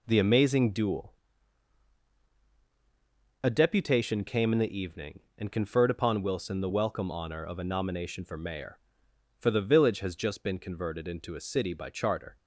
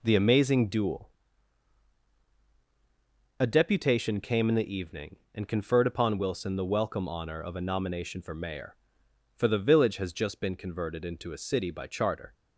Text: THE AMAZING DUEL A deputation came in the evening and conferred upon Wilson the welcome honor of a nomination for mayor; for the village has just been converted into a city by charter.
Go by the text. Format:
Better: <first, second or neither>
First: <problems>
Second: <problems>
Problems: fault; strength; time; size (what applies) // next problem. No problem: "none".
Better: neither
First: pauses between "DUEL" and "A"; strong; at 1.1 s; 2.2 s long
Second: pauses between "DUEL" and "A"; strong; at 1.1 s; 2.2 s long